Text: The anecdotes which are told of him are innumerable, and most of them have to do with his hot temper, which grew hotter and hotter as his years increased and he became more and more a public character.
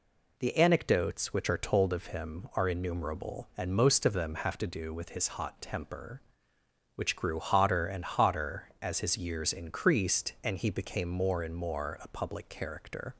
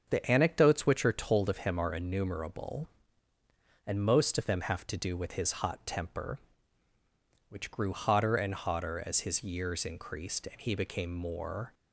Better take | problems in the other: first | starts louder than the rest; until 1.1 s; 6.5 dB // stops before "and more a public character"; at 11.7 s

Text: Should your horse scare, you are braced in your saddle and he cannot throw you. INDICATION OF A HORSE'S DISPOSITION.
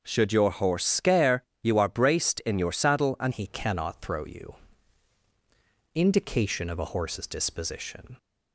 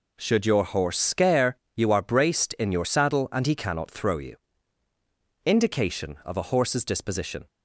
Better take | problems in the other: second | changes voice at "he"; from 3.3 s on; 4.8 s long

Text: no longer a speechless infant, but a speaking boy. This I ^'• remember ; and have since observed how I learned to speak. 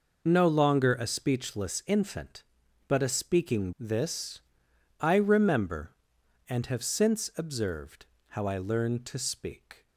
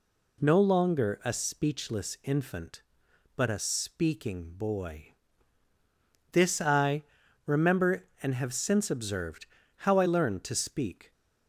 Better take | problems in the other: second | skips "boy"; at 3.7 s // pauses between "This" and "I"; noticeable; at 4.4 s; 0.60 s long // pauses between "observed" and "how"; slight; at 8.0 s; 0.24 s long; slight in the second

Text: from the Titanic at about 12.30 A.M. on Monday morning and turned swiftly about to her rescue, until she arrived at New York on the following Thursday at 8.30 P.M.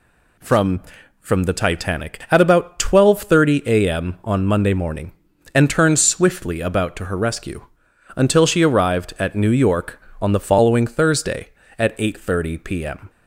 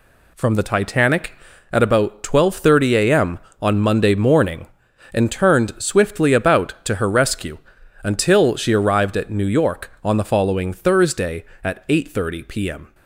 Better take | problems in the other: second | says "from" twice; at 1.1 s

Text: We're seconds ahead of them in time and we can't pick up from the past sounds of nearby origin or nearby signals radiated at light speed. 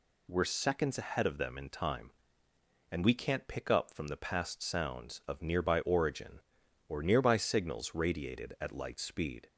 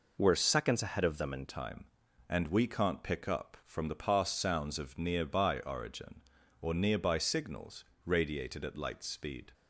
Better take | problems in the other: first | changes voice at "time"; from 1.4 s on; 8.1 s long // pauses between "signals" and "radiated"; slight; at 7.8 s; 0.22 s long

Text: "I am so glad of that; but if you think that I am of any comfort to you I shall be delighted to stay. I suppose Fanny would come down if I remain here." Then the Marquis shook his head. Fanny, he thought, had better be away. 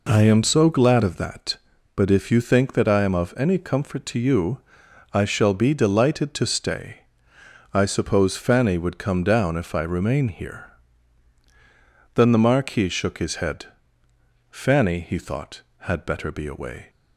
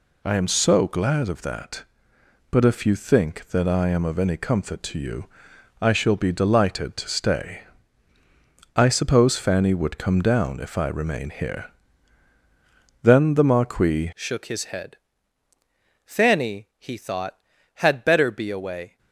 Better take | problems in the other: first | pauses between "you" and "I"; noticeable; at 5.2 s; 0.56 s long; noticeable in the first // changes voice at "shook"; from 14.1 s on; 4.8 s long

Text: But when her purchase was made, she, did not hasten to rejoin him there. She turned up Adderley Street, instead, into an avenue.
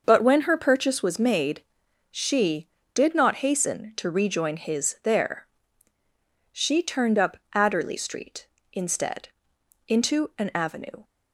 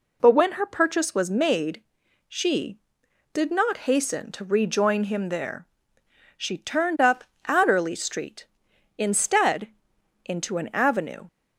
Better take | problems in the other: second | starts louder than the rest; until 1.0 s; 6 dB // says "his" for "him"; at 4.5 s // pauses between "up" and "Adderley"; slight; at 7.3 s; 0.16 s long; slight in the second

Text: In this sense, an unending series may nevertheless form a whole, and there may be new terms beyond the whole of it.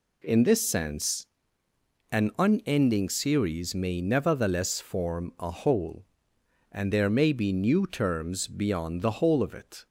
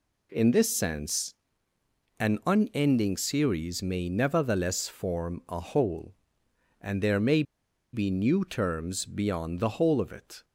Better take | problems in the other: first | pauses between "may" and "be"; noticeable; at 7.4 s; 0.50 s long

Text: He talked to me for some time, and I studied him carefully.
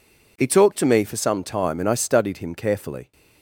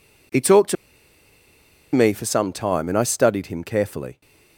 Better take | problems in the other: first | pauses between "to" and "me"; at 0.7 s; 1.1 s long

